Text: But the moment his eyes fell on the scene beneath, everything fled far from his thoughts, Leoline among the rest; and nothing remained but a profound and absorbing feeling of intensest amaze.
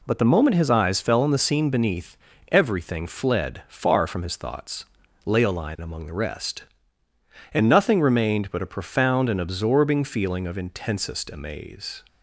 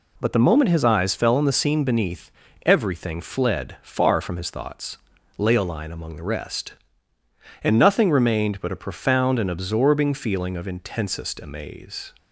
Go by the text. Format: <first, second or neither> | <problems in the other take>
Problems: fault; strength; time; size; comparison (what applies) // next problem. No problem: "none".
neither | none